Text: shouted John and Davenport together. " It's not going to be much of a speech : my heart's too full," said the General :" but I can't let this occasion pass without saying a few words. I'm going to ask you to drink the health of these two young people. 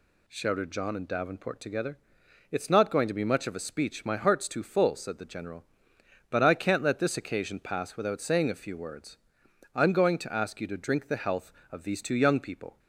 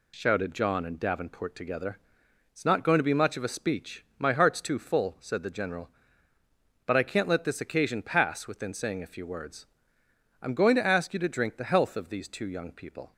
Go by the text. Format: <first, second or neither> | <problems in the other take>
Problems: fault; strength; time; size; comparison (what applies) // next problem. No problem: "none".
first | says "within" for "without"; at 8.4 s